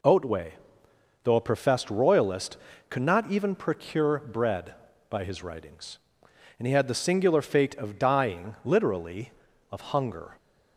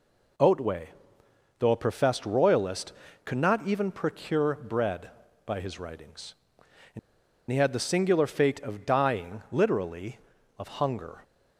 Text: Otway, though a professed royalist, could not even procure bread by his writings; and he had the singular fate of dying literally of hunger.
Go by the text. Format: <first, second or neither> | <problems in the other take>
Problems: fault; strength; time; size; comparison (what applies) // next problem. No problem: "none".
first | pauses between "and" and "he"; noticeable; at 6.9 s; 0.51 s long